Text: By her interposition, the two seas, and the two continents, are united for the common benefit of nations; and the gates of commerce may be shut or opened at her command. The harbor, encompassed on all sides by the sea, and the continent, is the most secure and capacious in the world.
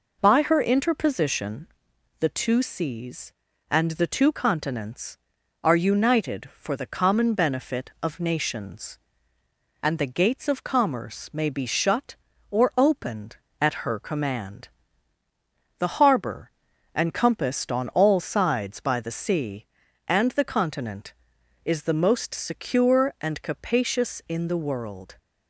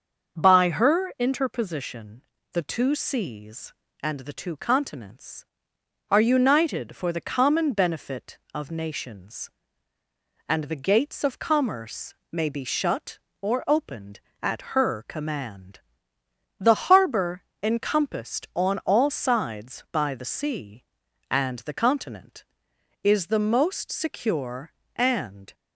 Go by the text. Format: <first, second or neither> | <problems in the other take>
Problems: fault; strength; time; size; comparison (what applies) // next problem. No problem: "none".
first | starts louder than the rest; until 1.4 s; 6.5 dB // pauses between "commerce" and "may"; slight; at 12.1 s; 0.18 s long // stops before "capacious in the world"; at 25.5 s